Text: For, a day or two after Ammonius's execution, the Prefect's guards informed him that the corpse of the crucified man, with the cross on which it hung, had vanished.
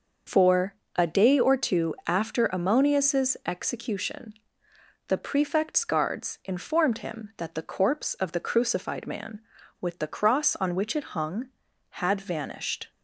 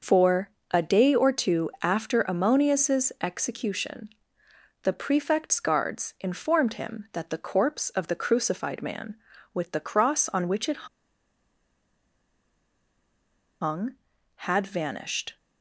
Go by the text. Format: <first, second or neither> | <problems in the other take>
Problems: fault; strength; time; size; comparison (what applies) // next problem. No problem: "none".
first | pauses between "it" and "hung"; strong; at 10.8 s; 2.7 s long